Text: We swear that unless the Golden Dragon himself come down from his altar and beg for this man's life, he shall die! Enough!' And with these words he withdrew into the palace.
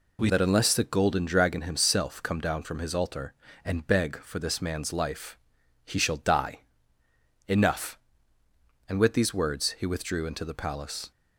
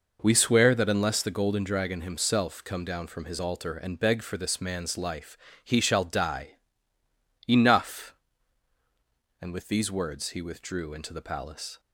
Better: second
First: skips "swear"; at 0.2 s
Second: none

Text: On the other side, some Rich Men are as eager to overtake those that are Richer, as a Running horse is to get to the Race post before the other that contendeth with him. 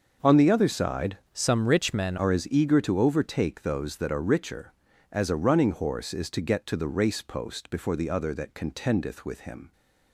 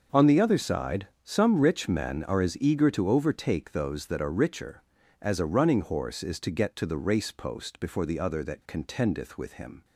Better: second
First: starts louder than the rest; until 1.4 s; 6.5 dB // changes voice from "some" to "Men"; from 1.3 to 2.1 s; 0.8 s long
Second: starts louder than the rest; until 1.3 s; 6 dB

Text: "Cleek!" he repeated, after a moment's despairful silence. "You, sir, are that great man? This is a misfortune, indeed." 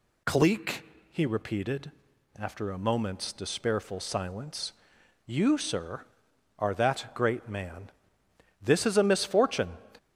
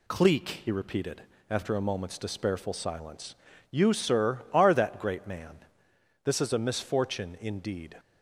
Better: second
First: stops before "indeed"; at 9.9 s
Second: none

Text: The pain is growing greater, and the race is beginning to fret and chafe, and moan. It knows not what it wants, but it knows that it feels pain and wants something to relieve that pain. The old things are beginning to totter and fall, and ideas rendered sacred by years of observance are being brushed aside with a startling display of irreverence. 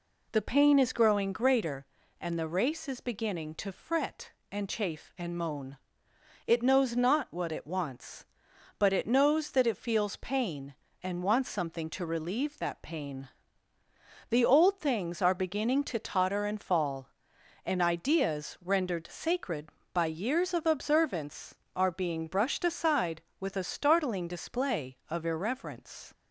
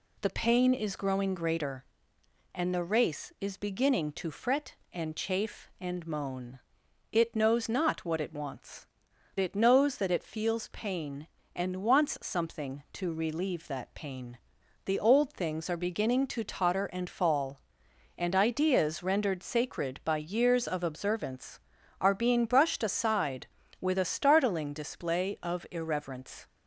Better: first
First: none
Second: skips "but"; at 9.1 s

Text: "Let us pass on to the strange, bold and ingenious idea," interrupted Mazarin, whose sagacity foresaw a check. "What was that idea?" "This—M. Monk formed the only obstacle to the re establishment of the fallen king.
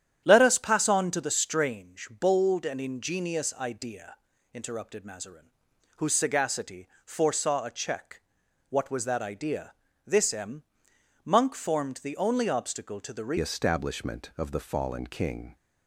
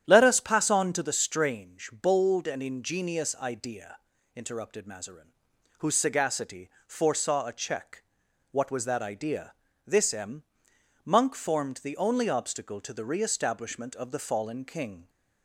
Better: second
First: starts louder than the rest; strong; until 1.2 s; 10 dB // pauses between "sagacity" and "foresaw"; slight; at 6.8 s; 0.16 s long // changes voice at "establishment"; from 13.3 s on; 2.2 s long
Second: starts louder than the rest; strong; until 1.0 s; 10 dB // pauses between "sagacity" and "foresaw"; slight; at 6.7 s; 0.16 s long

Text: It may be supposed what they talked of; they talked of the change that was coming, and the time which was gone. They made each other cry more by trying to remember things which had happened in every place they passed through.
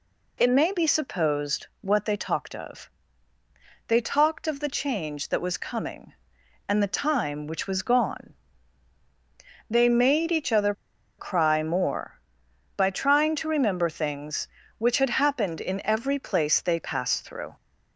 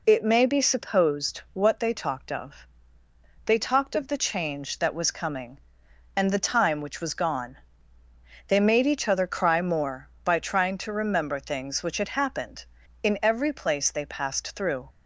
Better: second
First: pauses between "other" and "cry"; at 10.7 s; 0.45 s long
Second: none

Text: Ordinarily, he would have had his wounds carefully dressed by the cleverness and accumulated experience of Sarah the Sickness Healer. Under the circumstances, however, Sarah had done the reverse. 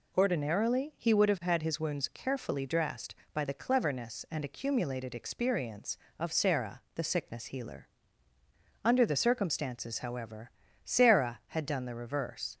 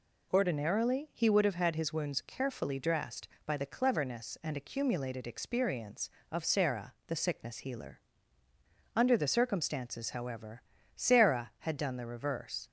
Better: neither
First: none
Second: none

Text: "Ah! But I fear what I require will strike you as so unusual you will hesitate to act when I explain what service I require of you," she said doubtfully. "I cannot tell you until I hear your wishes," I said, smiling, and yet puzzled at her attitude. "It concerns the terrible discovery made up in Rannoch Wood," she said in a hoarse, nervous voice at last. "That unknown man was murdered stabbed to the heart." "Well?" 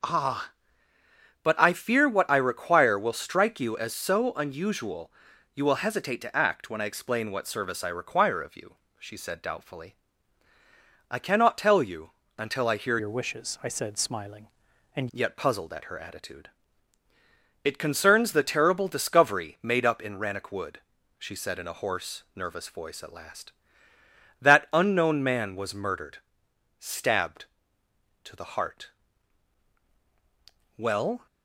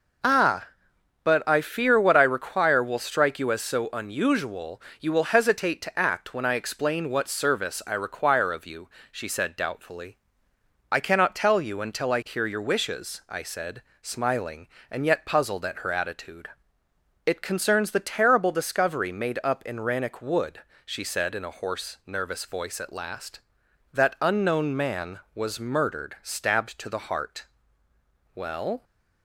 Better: second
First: pauses between "unusual" and "you"; at 5.1 s; 0.44 s long // pauses between "you" and "until"; slight; at 12.1 s; 0.26 s long // changes voice from "your" to "and"; from 12.9 to 15.0 s; 2.1 s long // pauses between "murdered" and "stabbed"; noticeable; at 26.1 s; 0.60 s long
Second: pauses between "unusual" and "you"; slight; at 4.8 s; 0.20 s long

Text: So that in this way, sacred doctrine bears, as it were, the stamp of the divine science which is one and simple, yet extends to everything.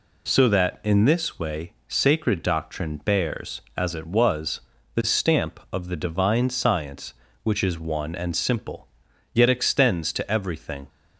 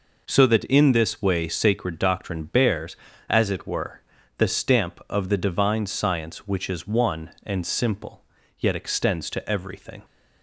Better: second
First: says "was" for "were"; at 4.0 s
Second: none

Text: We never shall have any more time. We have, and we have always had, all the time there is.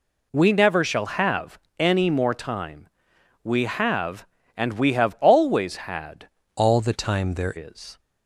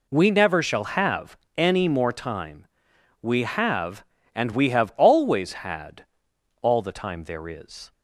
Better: second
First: pauses between "have" and "any"; slight; at 1.5 s; 0.22 s long // changes voice from "all" to "there"; from 6.5 to 7.5 s; 1.0 s long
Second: pauses between "have" and "any"; slight; at 1.3 s; 0.22 s long

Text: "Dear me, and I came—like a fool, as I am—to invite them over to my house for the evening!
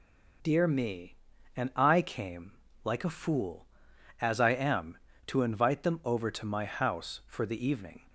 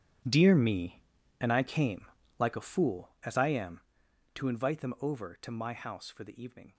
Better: first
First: none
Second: gets quieter; strong; throughout; 15 dB

